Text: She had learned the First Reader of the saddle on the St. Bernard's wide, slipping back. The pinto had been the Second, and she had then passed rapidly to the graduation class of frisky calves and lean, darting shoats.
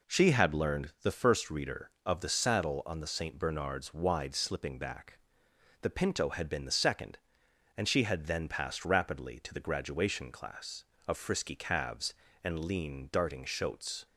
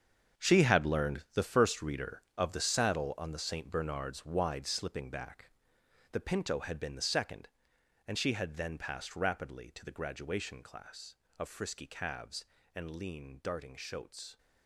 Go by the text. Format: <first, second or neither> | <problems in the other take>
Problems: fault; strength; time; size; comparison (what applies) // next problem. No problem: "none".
first | gets quieter; strong; throughout; 12.5 dB